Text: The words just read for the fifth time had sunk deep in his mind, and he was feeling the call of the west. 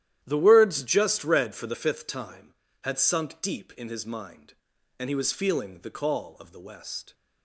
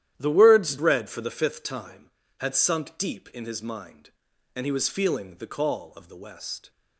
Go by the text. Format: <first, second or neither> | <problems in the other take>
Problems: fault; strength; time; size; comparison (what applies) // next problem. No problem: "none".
first | starts louder than the rest; strong; until 1.1 s; 11.5 dB; strong in the first // skips "just"; at 0.7 s